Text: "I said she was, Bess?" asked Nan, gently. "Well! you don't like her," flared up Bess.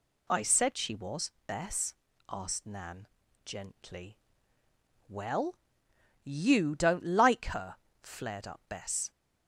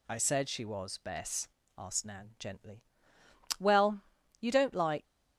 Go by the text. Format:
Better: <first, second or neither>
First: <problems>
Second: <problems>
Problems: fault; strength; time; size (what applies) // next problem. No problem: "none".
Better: first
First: none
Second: stops before "her flared up Bess"; at 5.0 s